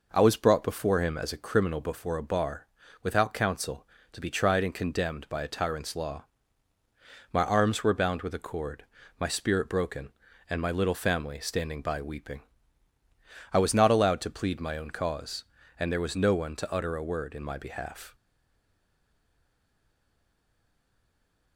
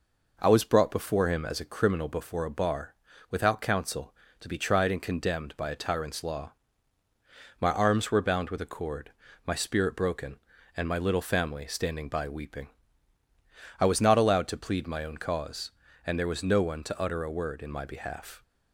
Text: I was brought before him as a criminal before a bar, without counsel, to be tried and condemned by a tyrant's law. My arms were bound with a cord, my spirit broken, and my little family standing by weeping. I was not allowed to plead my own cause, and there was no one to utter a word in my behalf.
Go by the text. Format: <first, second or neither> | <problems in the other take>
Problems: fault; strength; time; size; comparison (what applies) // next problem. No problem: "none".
second | stays silent after the last word; strong; from 18.1 s on; 3.4 s long